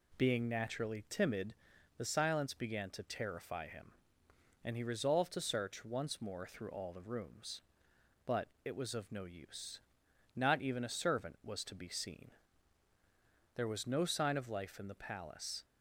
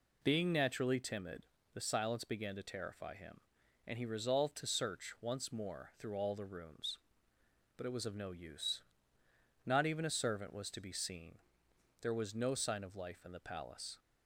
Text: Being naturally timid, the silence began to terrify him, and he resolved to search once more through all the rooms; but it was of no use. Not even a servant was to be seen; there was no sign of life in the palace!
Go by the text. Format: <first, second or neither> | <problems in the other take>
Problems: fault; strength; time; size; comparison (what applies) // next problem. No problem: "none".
neither | none